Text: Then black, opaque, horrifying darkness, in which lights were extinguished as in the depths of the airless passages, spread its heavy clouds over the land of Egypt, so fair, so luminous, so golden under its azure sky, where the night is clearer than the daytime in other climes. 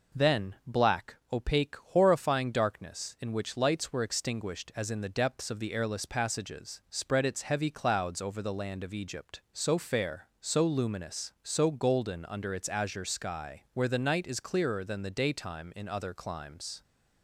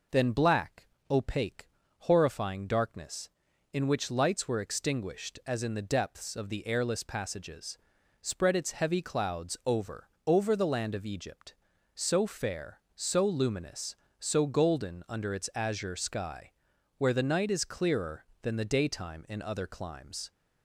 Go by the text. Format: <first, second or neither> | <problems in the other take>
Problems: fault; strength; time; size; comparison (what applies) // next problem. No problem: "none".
first | says "over" twice; at 10.2 s